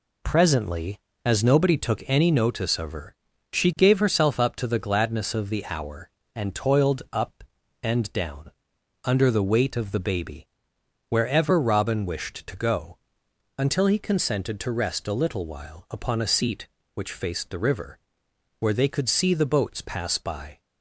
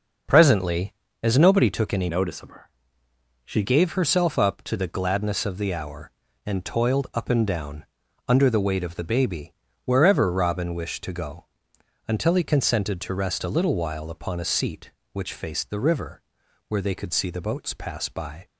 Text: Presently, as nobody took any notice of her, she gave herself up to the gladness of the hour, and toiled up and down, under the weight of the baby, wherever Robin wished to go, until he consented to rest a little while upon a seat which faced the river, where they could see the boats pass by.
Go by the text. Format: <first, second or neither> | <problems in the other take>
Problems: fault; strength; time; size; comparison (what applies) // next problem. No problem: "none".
first | changes voice from "notice" to "she"; from 2.0 to 3.6 s; 1.6 s long